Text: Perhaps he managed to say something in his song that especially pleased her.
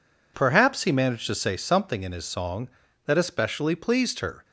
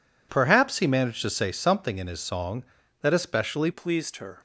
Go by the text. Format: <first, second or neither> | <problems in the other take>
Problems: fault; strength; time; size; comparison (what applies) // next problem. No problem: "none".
first | changes voice at "pleased"; from 3.7 s on; 0.6 s long